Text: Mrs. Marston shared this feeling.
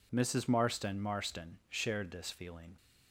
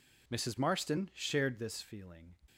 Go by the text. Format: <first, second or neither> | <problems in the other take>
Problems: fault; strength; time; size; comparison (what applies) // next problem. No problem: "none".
second | says "Marston" twice; at 1.0 s